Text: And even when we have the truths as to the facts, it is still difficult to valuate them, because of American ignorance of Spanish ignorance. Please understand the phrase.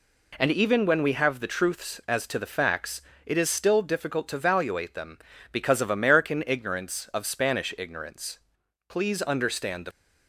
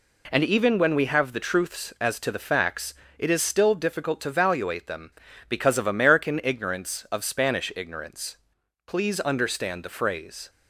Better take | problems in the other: second | stops before "phrase"; at 9.9 s

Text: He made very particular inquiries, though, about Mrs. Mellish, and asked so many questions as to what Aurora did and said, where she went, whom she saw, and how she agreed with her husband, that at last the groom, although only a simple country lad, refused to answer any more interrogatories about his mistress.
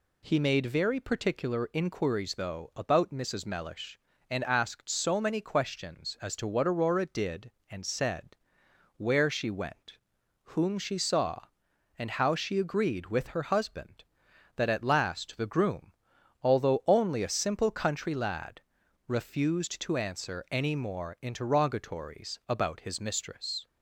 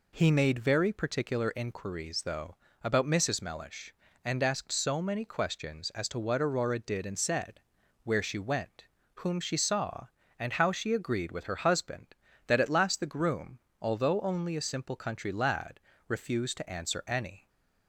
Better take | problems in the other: first | stops before "more interrogatories about his mistress"; at 17.4 s

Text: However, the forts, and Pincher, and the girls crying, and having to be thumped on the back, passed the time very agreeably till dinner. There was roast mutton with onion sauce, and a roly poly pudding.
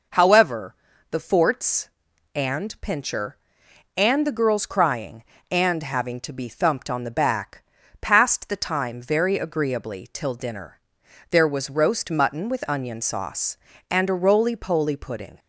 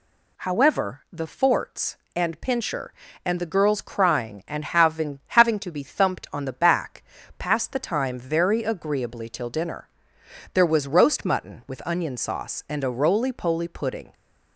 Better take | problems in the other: first | says "having" twice; at 5.2 s

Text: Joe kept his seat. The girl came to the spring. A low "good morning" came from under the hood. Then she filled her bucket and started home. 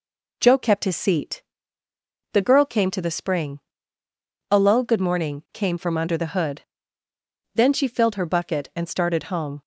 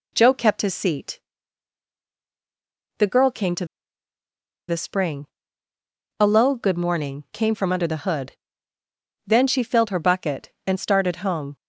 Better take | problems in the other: first | pauses between "to" and "the"; at 3.6 s; 1.0 s long

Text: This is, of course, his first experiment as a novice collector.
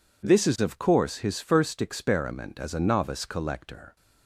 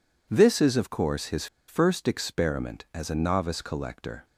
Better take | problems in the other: first | pauses between "his" and "first"; slight; at 1.4 s; 0.22 s long

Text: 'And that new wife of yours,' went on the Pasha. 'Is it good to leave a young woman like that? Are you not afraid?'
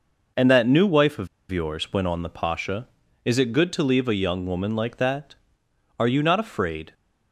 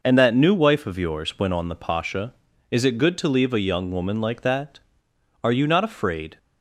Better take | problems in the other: second | pauses between "of" and "yours"; slight; at 1.2 s; 0.23 s long

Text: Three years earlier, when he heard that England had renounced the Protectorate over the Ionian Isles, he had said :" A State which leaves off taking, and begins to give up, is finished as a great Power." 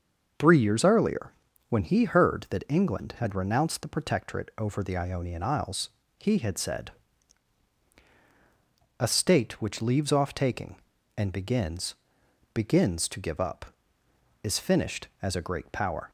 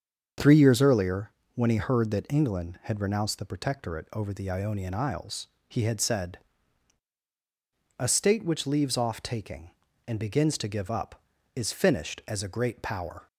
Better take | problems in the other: second | starts louder than the rest; until 1.7 s; 7 dB; strong in the second // says "begins" twice; at 12.5 s

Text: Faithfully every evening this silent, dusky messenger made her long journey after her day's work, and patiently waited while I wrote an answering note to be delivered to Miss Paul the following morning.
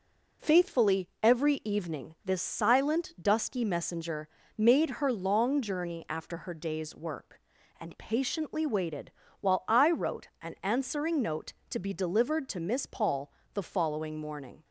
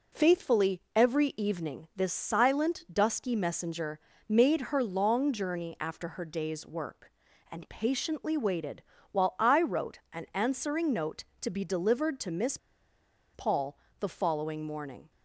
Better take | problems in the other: first | pauses between "messenger" and "made"; slight; at 3.9 s; 0.32 s long; slight in the first // pauses between "waited" and "while"; slight; at 8.8 s; 0.28 s long; slight in the first // pauses between "Miss" and "Paul"; noticeable; at 12.5 s; 0.77 s long // pauses between "Paul" and "the"; slight; at 13.7 s; 0.24 s long; slight in the first

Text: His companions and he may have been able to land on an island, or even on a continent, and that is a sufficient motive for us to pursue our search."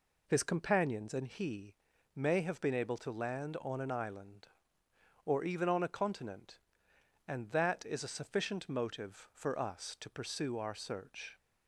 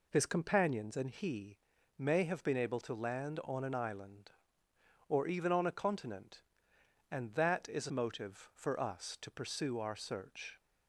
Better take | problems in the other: first | pauses between "he" and "may"; at 1.5 s; 0.40 s long; also in the first // skips "sufficient"; at 7.8 s

